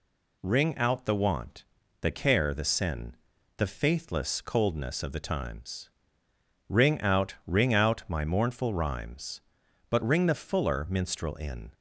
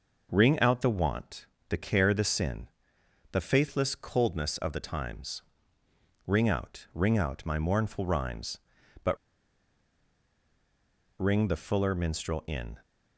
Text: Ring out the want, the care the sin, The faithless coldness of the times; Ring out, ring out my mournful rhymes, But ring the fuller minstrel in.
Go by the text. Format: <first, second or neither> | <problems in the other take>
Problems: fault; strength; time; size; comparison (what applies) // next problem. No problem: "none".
first | pauses between "But" and "ring"; strong; at 9.1 s; 2.0 s long